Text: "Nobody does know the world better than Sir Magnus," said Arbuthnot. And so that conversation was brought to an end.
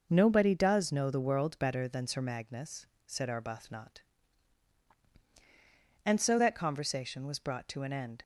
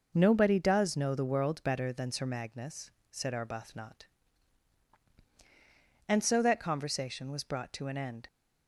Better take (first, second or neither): neither